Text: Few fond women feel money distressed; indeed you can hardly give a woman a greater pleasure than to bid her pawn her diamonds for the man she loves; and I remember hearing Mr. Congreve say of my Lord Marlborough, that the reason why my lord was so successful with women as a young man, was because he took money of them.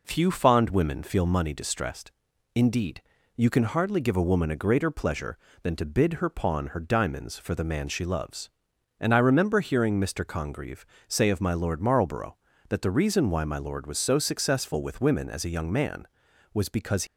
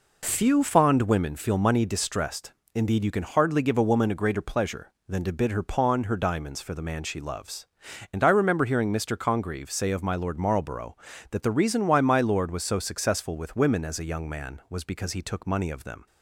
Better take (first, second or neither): second